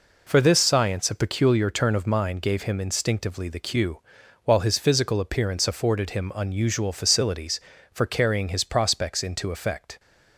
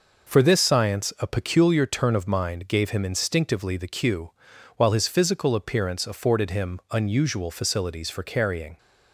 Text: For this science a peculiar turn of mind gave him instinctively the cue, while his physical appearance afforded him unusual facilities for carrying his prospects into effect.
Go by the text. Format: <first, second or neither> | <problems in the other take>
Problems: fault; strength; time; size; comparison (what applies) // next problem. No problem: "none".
first | stops before "his prospects into effect"; at 8.7 s